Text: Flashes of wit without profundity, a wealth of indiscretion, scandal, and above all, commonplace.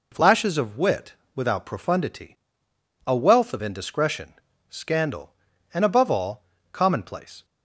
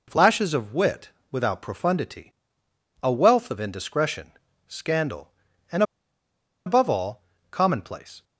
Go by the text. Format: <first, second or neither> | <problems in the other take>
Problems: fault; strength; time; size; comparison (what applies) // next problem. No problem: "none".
first | pauses between "wit" and "without"; slight; at 1.1 s; 0.20 s long; slight in the first // pauses between "and" and "above"; noticeable; at 5.8 s; 0.83 s long